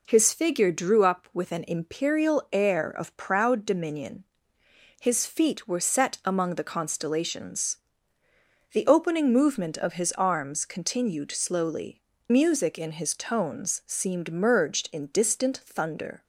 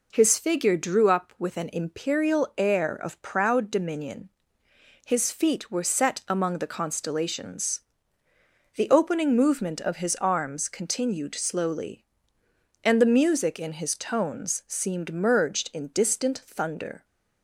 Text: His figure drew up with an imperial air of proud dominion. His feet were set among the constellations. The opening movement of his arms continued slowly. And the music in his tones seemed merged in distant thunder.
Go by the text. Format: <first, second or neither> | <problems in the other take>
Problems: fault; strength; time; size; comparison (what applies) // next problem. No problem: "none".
second | skips "And the"; at 12.1 s